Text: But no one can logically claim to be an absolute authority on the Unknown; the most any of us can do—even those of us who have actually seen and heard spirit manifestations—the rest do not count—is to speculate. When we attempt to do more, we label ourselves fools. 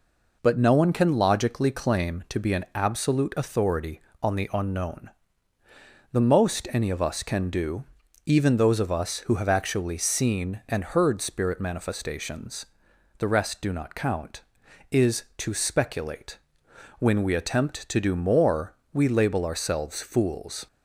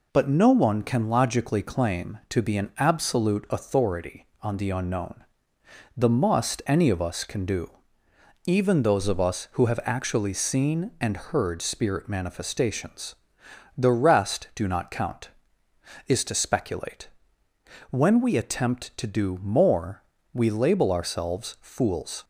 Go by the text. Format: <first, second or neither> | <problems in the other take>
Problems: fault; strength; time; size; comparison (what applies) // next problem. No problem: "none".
first | says "must" for "most"; at 6.0 s